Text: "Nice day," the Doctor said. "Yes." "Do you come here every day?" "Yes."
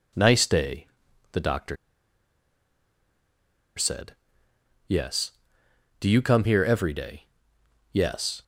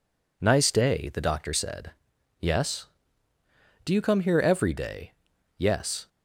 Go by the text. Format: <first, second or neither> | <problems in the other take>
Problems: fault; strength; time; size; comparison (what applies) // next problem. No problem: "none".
second | pauses between "Doctor" and "said"; strong; at 1.7 s; 2.0 s long